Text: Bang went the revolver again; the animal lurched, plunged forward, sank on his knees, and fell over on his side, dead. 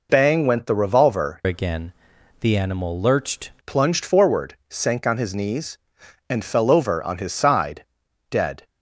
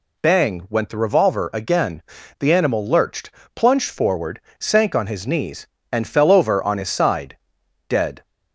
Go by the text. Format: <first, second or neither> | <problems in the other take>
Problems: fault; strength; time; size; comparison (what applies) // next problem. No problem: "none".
second | changes voice from "again" to "lurched"; from 1.4 to 3.5 s; 2.1 s long